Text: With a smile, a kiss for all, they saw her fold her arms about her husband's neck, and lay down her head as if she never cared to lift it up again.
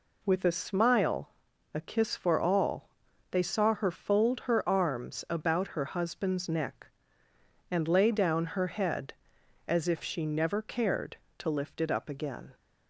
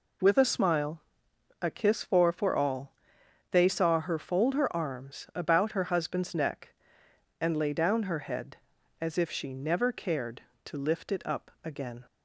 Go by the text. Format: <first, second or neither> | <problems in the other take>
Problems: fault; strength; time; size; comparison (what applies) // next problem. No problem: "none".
first | says "for" twice; at 2.3 s